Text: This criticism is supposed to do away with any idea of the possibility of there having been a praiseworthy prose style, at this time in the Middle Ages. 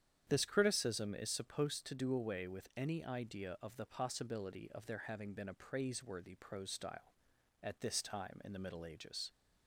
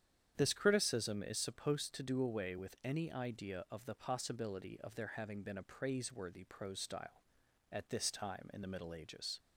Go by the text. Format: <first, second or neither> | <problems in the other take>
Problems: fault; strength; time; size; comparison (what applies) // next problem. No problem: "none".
neither | starts louder than the rest; strong; the same in both